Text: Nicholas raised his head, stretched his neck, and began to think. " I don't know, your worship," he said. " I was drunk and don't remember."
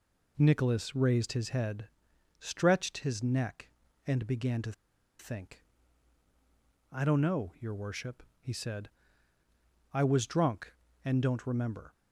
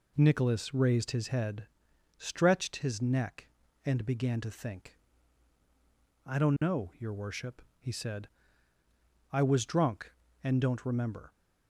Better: second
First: pauses between "to" and "think"; noticeable; at 4.7 s; 0.47 s long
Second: none

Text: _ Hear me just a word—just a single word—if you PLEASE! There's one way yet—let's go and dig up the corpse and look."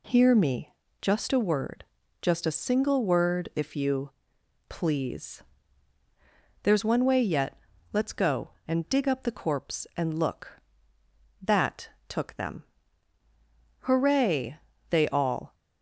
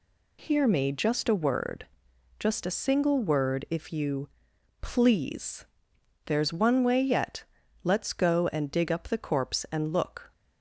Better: second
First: pauses between "me" and "just"; slight; at 0.7 s; 0.30 s long // pauses between "you" and "PLEASE"; noticeable; at 4.1 s; 0.58 s long // goes on to say "That took them Hooray they all"; strong; from 11.4 s on; 4.1 s long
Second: pauses between "you" and "PLEASE"; noticeable; at 4.2 s; 0.50 s long

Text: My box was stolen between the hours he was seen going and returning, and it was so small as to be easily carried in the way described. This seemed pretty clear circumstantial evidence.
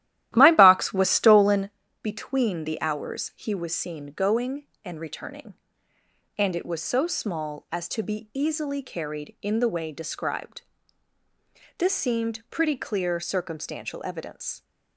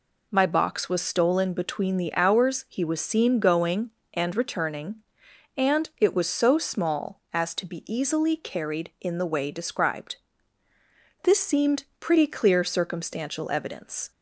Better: second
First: starts louder than the rest; strong; until 1.8 s; 13.5 dB // pauses between "stolen" and "between"; slight; at 1.6 s; 0.32 s long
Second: none

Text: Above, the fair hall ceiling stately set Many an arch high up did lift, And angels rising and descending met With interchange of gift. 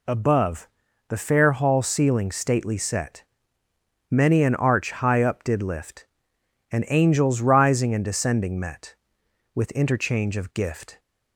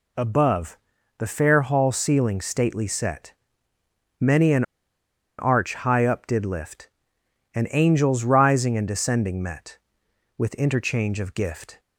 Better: first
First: pauses between "set" and "Many"; noticeable; at 3.2 s; 0.88 s long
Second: pauses between "set" and "Many"; noticeable; at 3.3 s; 0.88 s long // pauses between "an" and "arch"; noticeable; at 4.6 s; 0.76 s long

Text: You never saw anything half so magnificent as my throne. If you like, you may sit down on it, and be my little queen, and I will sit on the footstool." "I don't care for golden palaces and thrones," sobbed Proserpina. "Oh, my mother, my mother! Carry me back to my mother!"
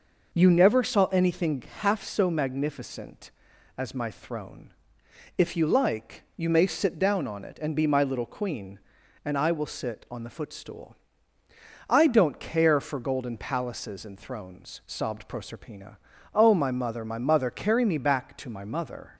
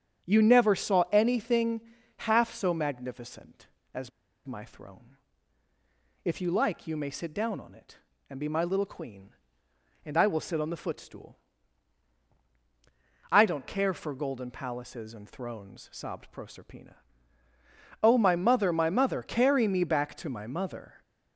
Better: first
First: pauses between "anything" and "half"; slight; at 1.6 s; 0.18 s long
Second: starts louder than the rest; strong; until 1.3 s; 8 dB // pauses between "anything" and "half"; slight; at 1.8 s; 0.36 s long // pauses between "as" and "my"; at 4.1 s; 0.37 s long

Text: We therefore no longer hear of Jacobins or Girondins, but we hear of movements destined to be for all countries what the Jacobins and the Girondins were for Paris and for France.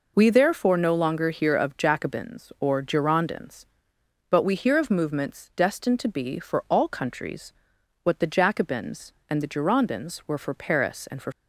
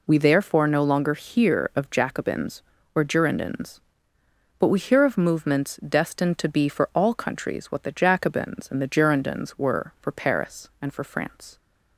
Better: second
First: pauses between "countries" and "what"; noticeable; at 7.5 s; 0.52 s long // stops before "France"; at 11.3 s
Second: none

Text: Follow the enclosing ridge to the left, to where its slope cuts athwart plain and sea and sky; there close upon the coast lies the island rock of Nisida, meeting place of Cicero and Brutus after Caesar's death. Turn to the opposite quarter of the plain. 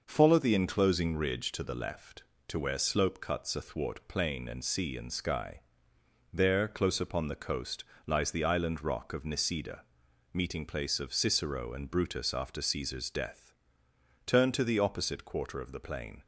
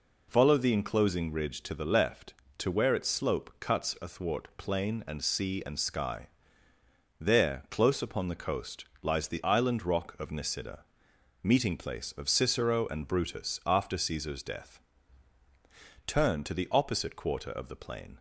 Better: second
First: skips "its"; at 2.7 s // pauses between "coast" and "lies"; slight; at 7.8 s; 0.22 s long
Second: pauses between "coast" and "lies"; slight; at 8.8 s; 0.16 s long

